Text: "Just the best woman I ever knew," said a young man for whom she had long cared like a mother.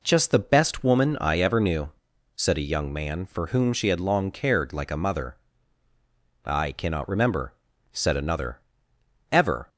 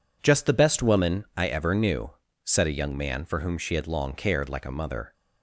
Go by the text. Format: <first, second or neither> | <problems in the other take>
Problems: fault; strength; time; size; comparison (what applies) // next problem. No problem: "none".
second | goes on to say "I cannot remember said another ever"; strong; from 6.4 s on; 3.2 s long